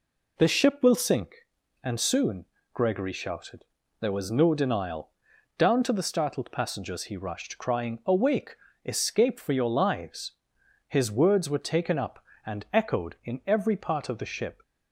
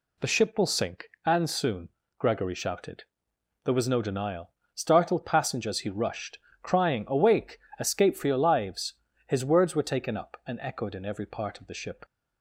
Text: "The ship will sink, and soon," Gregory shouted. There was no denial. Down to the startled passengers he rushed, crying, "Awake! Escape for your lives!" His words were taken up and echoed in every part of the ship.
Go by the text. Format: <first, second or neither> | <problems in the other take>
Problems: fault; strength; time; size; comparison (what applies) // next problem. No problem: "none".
first | skips "Down to the"; at 4.6 s